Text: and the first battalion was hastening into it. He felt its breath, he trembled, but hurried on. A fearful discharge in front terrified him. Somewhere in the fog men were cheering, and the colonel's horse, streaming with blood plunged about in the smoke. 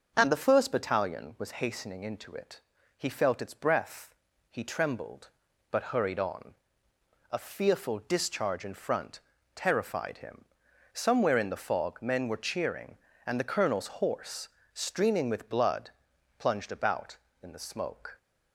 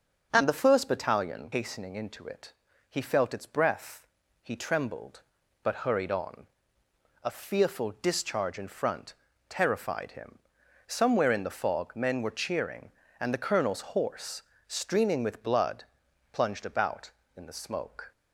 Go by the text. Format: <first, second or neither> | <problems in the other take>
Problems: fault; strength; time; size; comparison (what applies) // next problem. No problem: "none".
first | starts louder than the rest; until 1.3 s; 6.5 dB; also in the first // skips "was"; at 1.5 s // pauses between "front" and "terrified"; slight; at 9.1 s; 0.36 s long; slight in the first // pauses between "blood" and "plunged"; noticeable; at 15.8 s; 0.48 s long; noticeable in the first